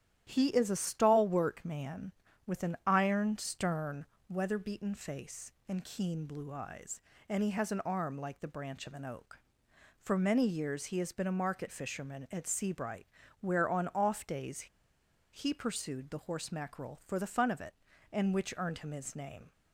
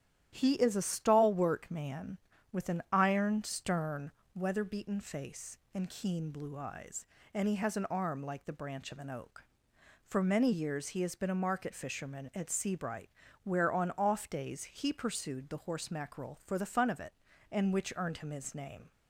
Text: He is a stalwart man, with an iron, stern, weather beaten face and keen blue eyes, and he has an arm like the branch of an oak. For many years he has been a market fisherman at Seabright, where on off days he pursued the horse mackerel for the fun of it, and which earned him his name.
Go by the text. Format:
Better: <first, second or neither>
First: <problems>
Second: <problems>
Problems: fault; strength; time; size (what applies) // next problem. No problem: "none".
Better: second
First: starts louder than the rest; strong; until 1.2 s; 11 dB // pauses between "days" and "he"; noticeable; at 14.6 s; 0.66 s long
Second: starts louder than the rest; strong; until 1.3 s; 11 dB